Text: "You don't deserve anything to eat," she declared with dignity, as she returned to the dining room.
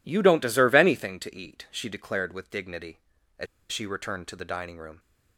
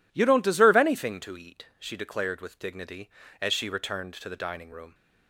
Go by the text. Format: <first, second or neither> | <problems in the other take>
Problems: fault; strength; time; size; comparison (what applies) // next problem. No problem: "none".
second | pauses between "as" and "she"; slight; at 3.4 s; 0.24 s long